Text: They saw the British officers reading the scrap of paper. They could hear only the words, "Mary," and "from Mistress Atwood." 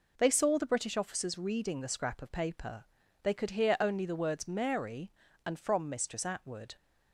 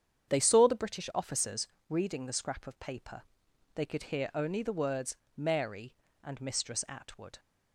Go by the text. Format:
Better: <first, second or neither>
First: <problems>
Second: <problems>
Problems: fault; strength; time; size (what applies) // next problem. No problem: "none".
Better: first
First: none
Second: starts louder than the rest; strong; until 1.3 s; 8 dB // pauses between "officers" and "reading"; slight; at 1.6 s; 0.22 s long // skips "from"; at 6.3 s